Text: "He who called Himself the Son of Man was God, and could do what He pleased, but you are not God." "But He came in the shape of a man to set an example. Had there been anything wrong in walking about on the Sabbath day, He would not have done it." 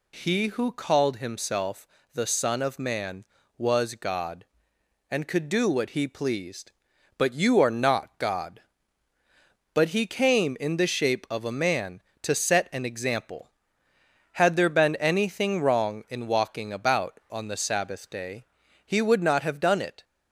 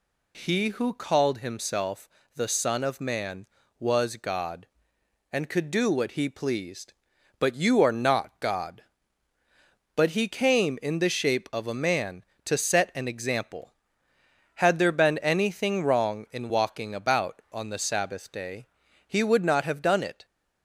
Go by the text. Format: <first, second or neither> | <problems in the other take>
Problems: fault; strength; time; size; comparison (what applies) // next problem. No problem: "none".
neither | pauses between "Himself" and "the"; slight; the same in both